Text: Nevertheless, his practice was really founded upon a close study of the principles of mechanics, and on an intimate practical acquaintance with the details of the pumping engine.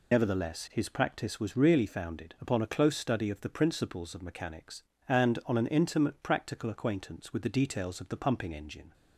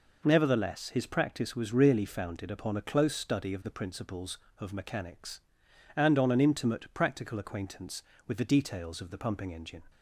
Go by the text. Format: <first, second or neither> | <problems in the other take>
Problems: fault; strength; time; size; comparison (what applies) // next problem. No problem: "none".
second | loses the start of "Nevertheless"; at 0.1 s; 45 ms